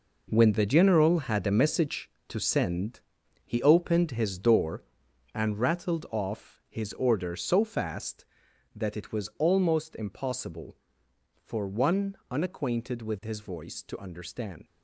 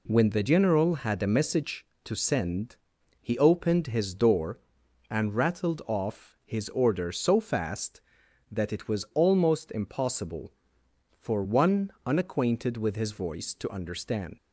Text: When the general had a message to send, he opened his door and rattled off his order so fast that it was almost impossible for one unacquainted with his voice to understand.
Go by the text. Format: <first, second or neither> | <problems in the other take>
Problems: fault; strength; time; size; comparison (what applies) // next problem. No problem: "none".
second | gets quieter; strong; throughout; 10.5 dB